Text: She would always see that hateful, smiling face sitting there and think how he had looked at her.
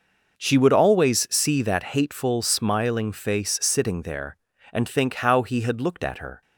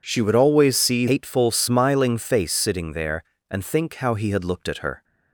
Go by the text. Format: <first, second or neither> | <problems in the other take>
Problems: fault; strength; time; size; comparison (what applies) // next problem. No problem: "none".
first | skips "that"; at 1.0 s